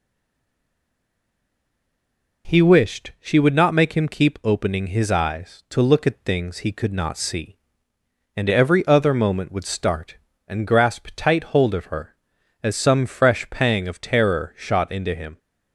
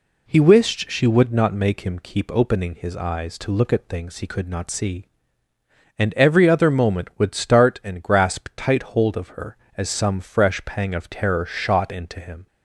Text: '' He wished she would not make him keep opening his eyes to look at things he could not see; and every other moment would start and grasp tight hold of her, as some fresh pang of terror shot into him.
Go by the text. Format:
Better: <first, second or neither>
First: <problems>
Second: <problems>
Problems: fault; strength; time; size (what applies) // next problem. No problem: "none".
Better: second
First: stays silent before the first word; until 2.4 s; 2.4 s long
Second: none